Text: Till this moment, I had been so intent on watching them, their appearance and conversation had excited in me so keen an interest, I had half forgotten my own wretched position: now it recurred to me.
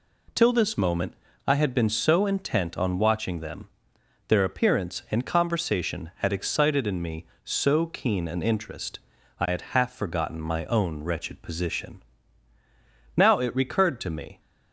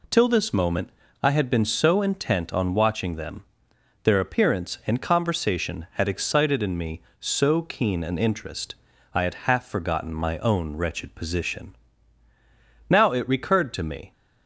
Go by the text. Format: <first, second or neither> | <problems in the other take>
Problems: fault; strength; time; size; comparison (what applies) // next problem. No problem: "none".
neither | none